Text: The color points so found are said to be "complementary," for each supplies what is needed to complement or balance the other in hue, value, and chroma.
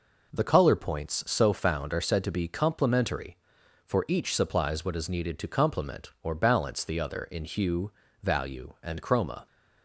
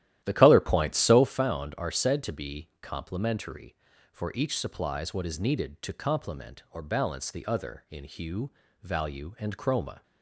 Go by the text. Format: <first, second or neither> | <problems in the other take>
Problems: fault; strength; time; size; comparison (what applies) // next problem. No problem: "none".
first | starts louder than the rest; strong; until 1.4 s; 13 dB